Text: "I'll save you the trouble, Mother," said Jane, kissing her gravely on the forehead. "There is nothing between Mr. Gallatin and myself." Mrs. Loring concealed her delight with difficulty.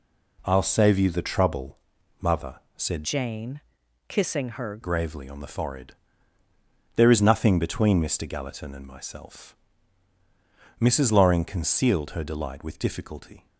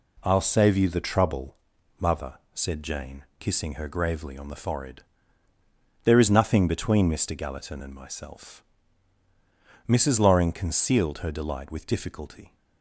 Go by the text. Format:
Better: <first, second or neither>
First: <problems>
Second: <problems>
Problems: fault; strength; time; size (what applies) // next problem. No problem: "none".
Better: second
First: changes voice from "Jane" to "her"; from 3.0 to 4.8 s; 1.8 s long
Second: none